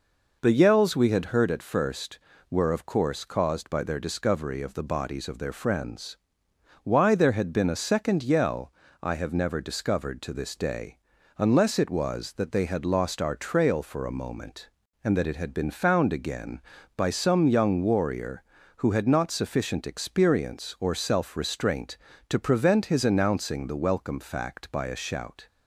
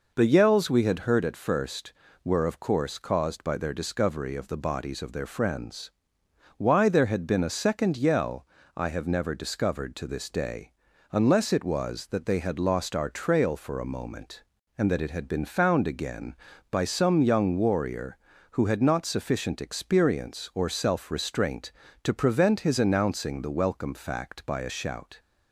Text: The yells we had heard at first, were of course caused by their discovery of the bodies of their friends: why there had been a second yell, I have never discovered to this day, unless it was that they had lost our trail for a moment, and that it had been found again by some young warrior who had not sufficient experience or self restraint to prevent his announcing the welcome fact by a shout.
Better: neither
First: none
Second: none

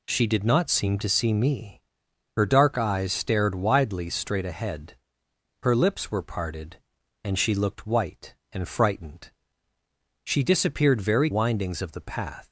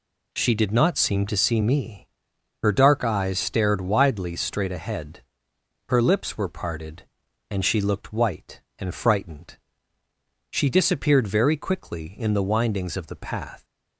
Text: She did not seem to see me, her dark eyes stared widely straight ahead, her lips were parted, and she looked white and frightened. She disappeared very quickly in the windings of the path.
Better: second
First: skips "quickly in the"; at 11.3 s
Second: none

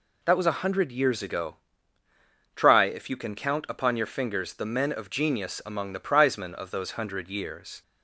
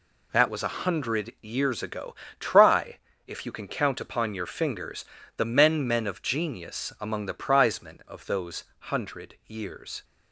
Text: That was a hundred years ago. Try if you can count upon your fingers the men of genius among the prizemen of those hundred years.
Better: first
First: none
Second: pauses between "Try" and "if"; slight; at 2.9 s; 0.28 s long // pauses between "fingers" and "the"; slight; at 5.0 s; 0.32 s long // says "men" twice; at 5.8 s

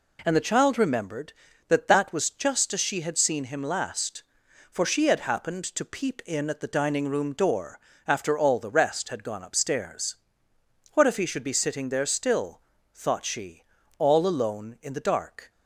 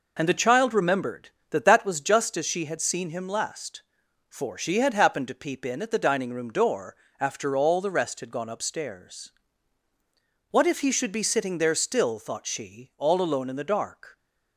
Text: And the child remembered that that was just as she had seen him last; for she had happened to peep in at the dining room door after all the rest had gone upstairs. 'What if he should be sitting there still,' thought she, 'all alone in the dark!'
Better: neither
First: pauses between "door" and "after"; slight; at 7.8 s; 0.26 s long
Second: pauses between "door" and "after"; slight; at 6.9 s; 0.24 s long

